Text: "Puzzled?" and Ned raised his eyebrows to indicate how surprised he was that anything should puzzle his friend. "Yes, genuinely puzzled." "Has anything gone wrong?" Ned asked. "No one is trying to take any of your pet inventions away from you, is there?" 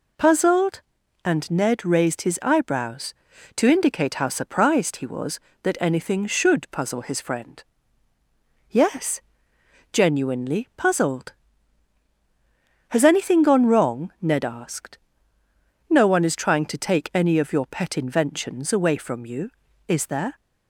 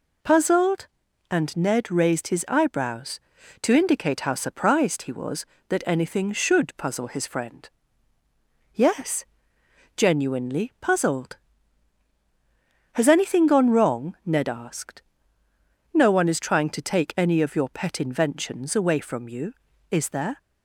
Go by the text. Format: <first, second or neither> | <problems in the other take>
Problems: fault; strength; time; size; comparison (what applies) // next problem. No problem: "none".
neither | none